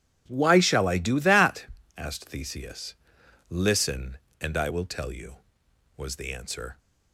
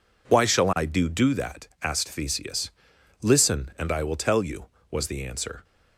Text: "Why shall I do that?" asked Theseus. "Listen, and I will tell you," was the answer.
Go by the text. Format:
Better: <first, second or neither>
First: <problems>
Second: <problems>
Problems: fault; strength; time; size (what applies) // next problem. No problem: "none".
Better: first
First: none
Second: says "do" twice; at 1.0 s